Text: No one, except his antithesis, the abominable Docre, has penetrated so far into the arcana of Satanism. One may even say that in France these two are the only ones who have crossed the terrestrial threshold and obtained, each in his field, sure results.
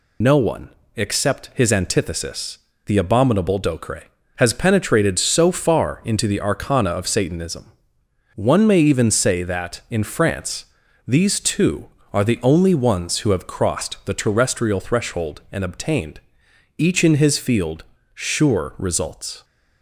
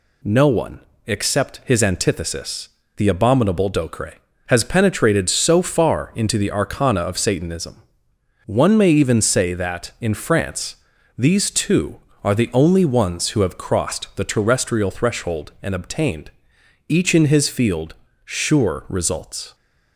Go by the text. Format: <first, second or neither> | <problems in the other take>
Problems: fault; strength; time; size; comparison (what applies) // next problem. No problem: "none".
second | loses the start of "No"; at 0.2 s; 70 ms // pauses between "France" and "these"; at 10.6 s; 0.42 s long; also in the second